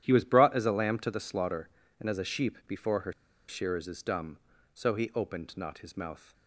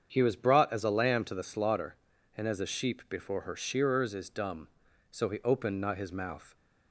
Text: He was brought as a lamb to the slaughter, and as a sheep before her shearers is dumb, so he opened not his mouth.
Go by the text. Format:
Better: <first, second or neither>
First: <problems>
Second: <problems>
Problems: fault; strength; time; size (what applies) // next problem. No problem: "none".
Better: second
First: starts louder than the rest; strong; until 1.0 s; 11 dB // pauses between "her" and "shearers"; at 3.1 s; 0.36 s long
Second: starts louder than the rest; strong; until 1.1 s; 7.5 dB